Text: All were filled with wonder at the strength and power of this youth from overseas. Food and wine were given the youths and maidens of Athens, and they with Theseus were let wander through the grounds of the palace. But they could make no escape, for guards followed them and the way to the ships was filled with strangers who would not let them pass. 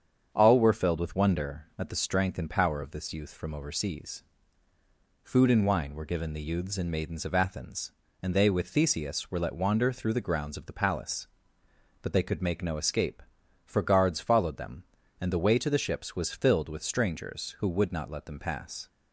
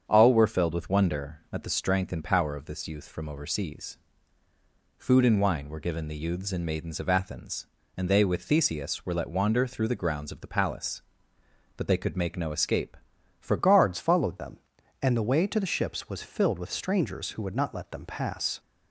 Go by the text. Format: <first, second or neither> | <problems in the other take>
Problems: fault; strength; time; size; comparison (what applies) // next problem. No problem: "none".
first | starts louder than the rest; strong; until 1.0 s; 7.5 dB; strong in the first // changes voice at "guards"; from 13.5 s on; 5.0 s long